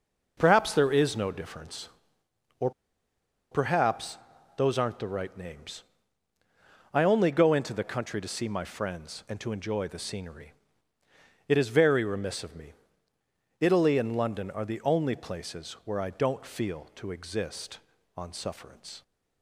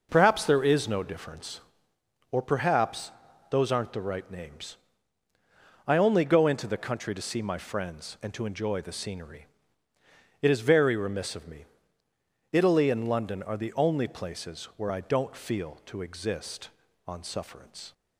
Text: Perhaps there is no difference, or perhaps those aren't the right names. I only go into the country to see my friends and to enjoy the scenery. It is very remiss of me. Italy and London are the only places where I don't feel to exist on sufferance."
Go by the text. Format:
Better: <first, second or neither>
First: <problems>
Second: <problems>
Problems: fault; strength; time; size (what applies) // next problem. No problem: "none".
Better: second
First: pauses between "or" and "perhaps"; noticeable; at 2.7 s; 0.81 s long // pauses between "perhaps" and "those"; at 4.1 s; 0.40 s long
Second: pauses between "perhaps" and "those"; at 3.1 s; 0.40 s long